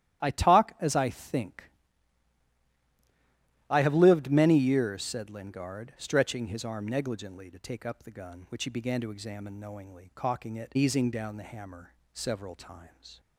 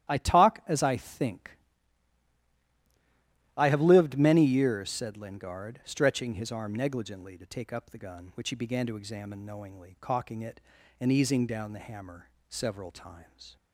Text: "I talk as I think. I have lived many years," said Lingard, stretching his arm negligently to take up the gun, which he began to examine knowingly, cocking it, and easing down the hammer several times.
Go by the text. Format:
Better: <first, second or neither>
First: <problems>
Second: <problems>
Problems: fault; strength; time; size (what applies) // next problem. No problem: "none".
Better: second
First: starts louder than the rest; strong; until 1.2 s; 12 dB // skips "and"; at 10.7 s // pauses between "hammer" and "several"; slight; at 11.9 s; 0.18 s long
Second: starts louder than the rest; strong; until 1.1 s; 12 dB // pauses between "hammer" and "several"; slight; at 12.2 s; 0.18 s long